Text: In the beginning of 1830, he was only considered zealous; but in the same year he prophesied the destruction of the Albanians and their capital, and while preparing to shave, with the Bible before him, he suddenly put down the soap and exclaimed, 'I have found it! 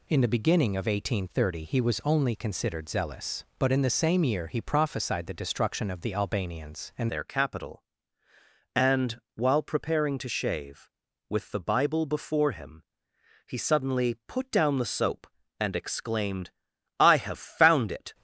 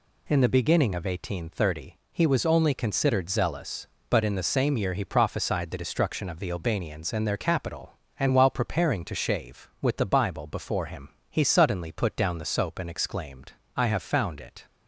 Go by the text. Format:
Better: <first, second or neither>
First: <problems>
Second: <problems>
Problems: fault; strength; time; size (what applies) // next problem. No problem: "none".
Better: second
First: changes voice at "their"; from 7.0 s on; 11.1 s long // pauses between "and" and "while"; slight; at 9.2 s; 0.16 s long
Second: none